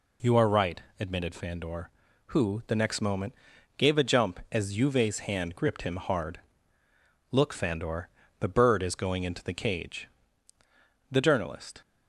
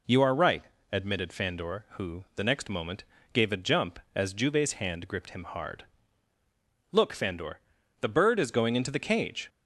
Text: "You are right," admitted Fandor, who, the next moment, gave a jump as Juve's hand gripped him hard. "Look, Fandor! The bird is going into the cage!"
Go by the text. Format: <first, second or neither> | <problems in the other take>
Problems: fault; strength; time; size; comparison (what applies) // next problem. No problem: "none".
second | goes on to say "The journalist"; noticeable; from 11.1 s on; 0.70 s long